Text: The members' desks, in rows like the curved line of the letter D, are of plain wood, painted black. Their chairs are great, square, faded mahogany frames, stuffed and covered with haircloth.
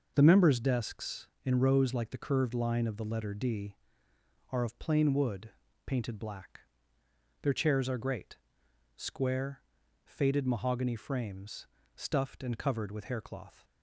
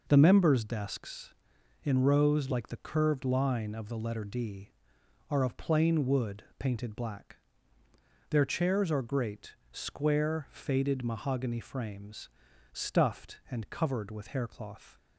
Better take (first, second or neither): neither